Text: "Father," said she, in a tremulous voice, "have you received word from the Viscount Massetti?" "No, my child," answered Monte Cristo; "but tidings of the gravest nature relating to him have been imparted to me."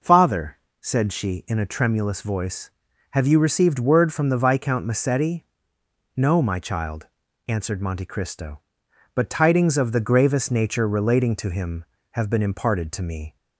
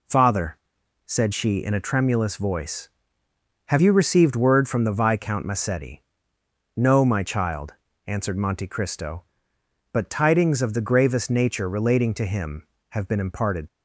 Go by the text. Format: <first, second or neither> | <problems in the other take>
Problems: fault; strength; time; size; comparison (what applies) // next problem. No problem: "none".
first | stops before "to me"; at 13.6 s